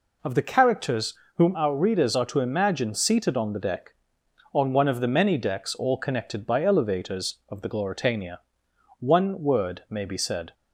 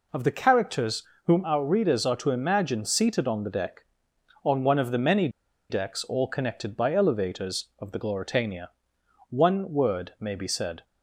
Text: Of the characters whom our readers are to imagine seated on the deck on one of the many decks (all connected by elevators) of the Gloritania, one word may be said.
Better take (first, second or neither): first